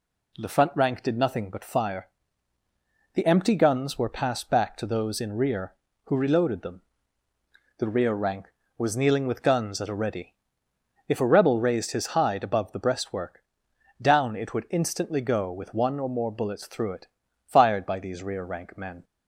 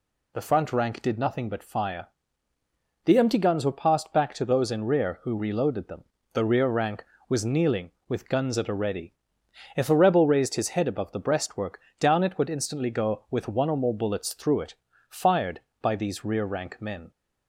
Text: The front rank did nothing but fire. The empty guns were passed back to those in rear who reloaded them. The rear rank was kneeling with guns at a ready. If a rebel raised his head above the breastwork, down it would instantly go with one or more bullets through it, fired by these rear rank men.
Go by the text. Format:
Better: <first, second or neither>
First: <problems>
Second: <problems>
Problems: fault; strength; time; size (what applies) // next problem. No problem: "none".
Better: second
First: says "hide" for "head"; at 12.0 s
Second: none